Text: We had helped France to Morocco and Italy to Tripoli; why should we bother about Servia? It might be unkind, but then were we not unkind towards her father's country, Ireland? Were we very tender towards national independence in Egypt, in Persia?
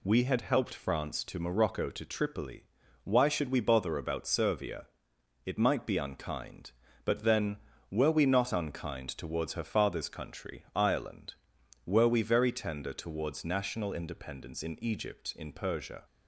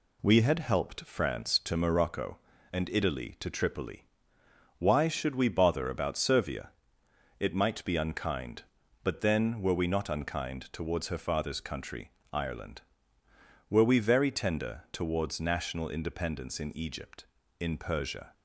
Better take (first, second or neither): second